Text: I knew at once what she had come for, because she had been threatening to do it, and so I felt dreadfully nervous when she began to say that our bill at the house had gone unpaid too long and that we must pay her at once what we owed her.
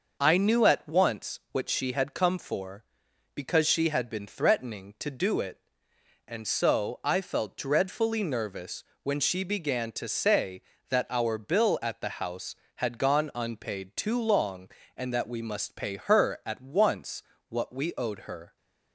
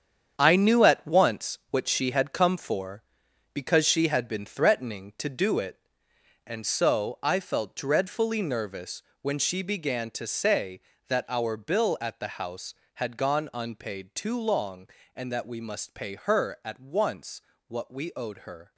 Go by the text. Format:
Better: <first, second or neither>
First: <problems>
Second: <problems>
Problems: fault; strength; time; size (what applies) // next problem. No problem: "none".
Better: first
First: pauses between "nervous" and "when"; slight; at 8.8 s; 0.20 s long // pauses between "once" and "what"; slight; at 17.2 s; 0.28 s long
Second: gets quieter; strong; throughout; 9.5 dB // pauses between "nervous" and "when"; slight; at 9.0 s; 0.20 s long // pauses between "once" and "what"; slight; at 17.4 s; 0.28 s long